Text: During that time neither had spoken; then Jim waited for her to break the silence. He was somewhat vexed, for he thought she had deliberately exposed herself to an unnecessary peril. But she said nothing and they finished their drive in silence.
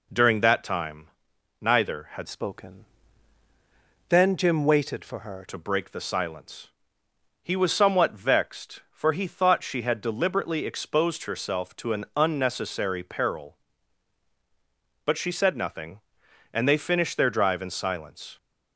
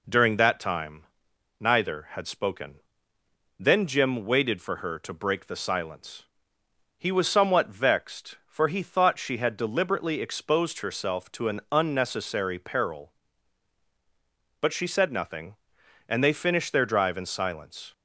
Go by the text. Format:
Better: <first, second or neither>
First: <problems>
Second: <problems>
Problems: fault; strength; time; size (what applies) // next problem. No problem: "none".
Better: second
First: pauses between "time" and "neither"; noticeable; at 1.0 s; 0.52 s long // changes voice from "spoken" to "her"; from 2.2 to 5.4 s; 3.2 s long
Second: pauses between "time" and "neither"; noticeable; at 1.0 s; 0.54 s long